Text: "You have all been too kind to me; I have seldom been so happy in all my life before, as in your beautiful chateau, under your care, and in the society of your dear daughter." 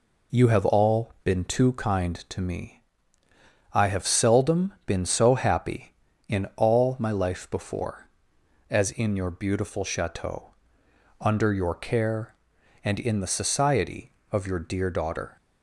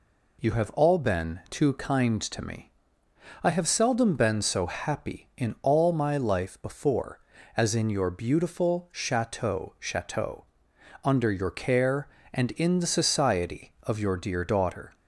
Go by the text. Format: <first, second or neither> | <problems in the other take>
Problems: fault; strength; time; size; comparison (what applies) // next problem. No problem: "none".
first | says "chateau" twice; at 9.7 s